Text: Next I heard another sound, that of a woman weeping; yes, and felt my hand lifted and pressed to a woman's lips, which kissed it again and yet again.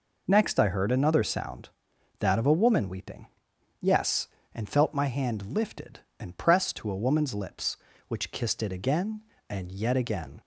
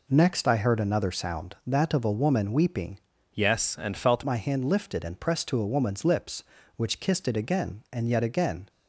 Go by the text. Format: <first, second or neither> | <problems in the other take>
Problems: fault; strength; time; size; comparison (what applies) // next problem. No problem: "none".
first | changes voice from "yes" to "felt"; from 3.3 to 4.2 s; 0.9 s long